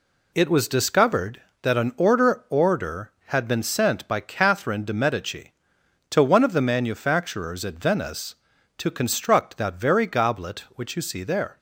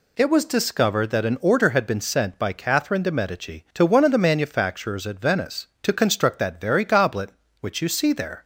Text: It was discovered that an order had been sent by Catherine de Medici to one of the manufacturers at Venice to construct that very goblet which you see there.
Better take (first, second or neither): second